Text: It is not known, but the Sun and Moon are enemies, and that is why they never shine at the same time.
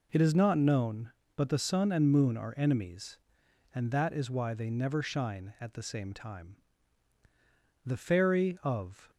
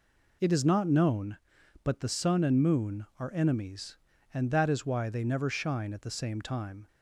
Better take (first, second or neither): second